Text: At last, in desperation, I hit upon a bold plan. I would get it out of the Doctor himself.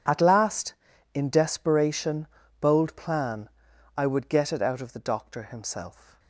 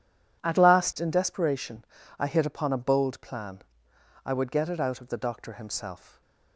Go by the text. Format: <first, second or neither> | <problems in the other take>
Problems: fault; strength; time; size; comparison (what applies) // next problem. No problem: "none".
second | skips "I hit upon a"; at 2.4 s